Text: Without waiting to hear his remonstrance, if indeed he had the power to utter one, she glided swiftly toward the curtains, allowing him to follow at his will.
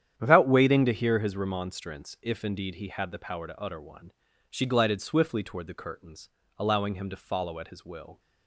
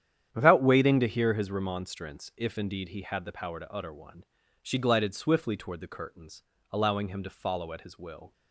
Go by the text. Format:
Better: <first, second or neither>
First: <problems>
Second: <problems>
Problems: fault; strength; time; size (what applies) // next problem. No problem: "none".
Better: neither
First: starts louder than the rest; strong; until 1.1 s; 10 dB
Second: starts louder than the rest; strong; until 1.3 s; 10 dB